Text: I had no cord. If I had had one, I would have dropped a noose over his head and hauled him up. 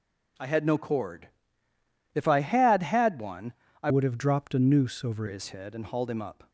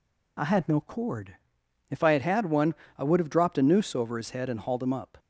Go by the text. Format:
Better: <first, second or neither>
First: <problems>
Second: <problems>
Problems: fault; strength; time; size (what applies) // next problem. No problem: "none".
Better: second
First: changes voice from "would" to "over"; from 3.8 to 5.2 s; 1.4 s long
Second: none